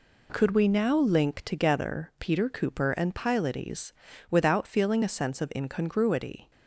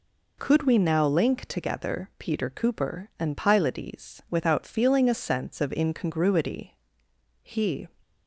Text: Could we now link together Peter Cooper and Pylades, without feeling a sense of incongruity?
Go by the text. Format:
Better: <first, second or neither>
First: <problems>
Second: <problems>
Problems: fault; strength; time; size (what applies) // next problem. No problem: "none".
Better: first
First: none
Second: goes on to say "He"; slight; from 7.4 s on; 0.46 s long